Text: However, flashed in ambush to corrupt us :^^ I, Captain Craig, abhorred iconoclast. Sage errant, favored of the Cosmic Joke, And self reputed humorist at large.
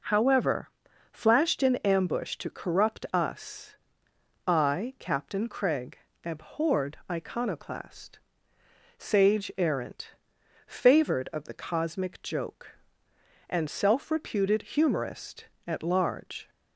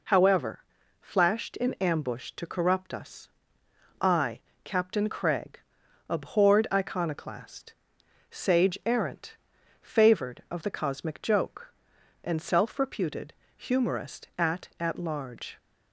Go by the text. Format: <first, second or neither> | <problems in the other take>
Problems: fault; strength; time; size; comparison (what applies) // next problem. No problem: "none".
first | pauses between "reputed" and "humorist"; slight; at 13.3 s; 0.24 s long // says "at" twice; at 14.7 s